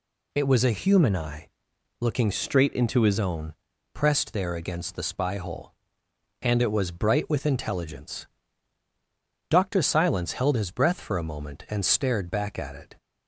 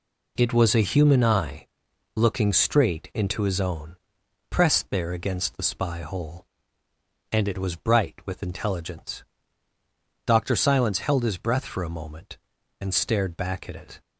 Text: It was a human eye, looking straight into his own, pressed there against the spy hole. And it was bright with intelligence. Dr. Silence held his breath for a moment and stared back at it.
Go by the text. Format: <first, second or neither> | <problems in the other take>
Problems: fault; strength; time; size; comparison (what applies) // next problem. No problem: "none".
second | changes voice from "straight" to "his"; from 2.3 to 3.1 s; 0.8 s long